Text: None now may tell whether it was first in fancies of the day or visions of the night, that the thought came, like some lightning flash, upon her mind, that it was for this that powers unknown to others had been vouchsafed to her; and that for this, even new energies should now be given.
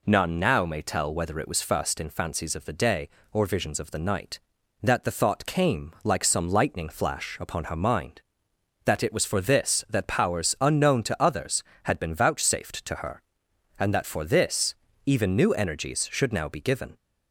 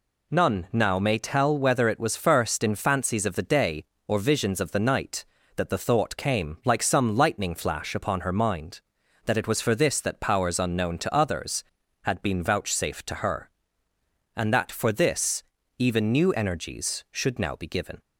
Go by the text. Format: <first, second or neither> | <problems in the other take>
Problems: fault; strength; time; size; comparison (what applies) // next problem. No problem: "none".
neither | none